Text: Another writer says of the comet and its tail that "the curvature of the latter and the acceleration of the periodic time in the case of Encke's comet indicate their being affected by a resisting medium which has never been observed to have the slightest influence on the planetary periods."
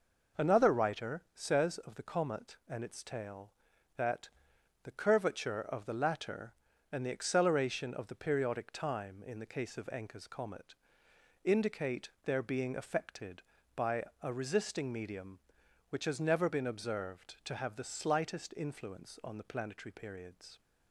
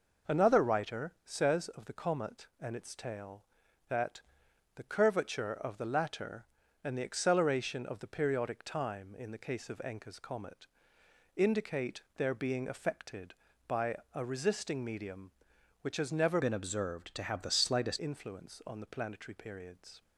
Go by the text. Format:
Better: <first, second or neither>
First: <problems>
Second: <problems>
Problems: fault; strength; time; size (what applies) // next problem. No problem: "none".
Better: first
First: pauses between "that" and "the"; noticeable; at 4.3 s; 0.54 s long // pauses between "comet" and "indicate"; noticeable; at 10.7 s; 0.70 s long // pauses between "indicate" and "their"; slight; at 12.0 s; 0.16 s long // pauses between "by" and "a"; slight; at 14.0 s; 0.18 s long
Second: pauses between "that" and "the"; noticeable; at 4.2 s; 0.54 s long // pauses between "comet" and "indicate"; noticeable; at 10.6 s; 0.70 s long // pauses between "indicate" and "their"; slight; at 12.0 s; 0.16 s long // pauses between "by" and "a"; slight; at 13.9 s; 0.18 s long // changes voice from "been" to "slightest"; from 16.4 to 17.9 s; 1.5 s long